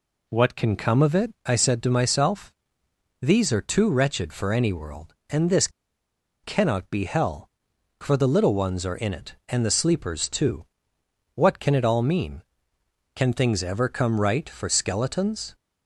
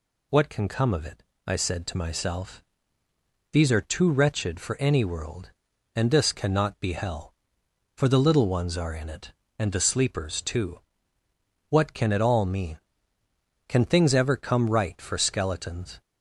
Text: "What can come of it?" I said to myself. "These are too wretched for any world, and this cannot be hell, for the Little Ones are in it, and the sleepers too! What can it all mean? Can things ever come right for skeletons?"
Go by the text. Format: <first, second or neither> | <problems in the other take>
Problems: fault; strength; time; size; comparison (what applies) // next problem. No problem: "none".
second | pauses between "this" and "cannot"; noticeable; at 5.6 s; 0.74 s long